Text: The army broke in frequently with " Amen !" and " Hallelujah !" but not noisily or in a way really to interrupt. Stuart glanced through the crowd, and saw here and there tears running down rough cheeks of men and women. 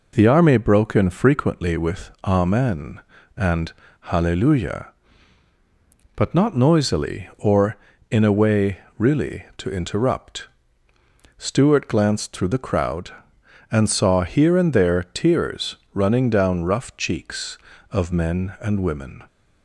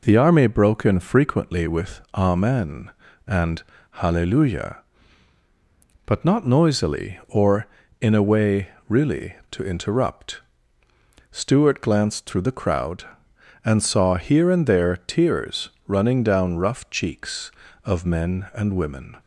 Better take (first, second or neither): neither